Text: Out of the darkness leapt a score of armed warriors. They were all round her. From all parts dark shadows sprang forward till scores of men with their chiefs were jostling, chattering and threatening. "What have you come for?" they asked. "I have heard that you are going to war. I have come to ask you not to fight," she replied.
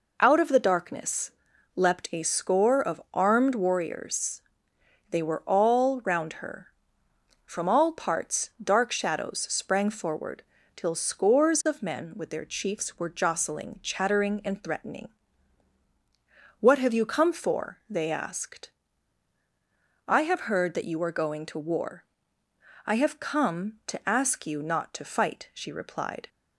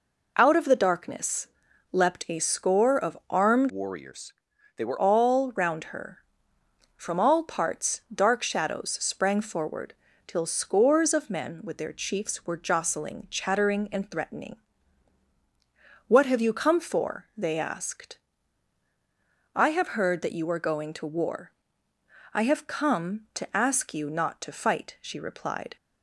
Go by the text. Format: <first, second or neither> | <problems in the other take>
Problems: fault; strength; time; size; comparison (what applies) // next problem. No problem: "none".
first | pauses between "darkness" and "leapt"; at 1.4 s; 0.44 s long; also in the first // changes voice from "warriors" to "were"; from 3.6 to 4.9 s; 1.3 s long // pauses between "forward" and "till"; slight; at 9.9 s; 0.32 s long; slight in the first